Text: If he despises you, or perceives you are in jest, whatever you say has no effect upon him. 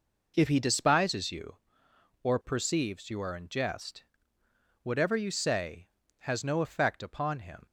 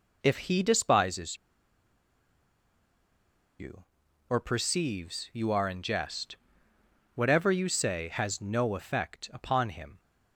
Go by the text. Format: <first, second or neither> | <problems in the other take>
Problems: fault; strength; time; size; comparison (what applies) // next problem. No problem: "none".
first | pauses between "despises" and "you"; strong; at 1.3 s; 2.2 s long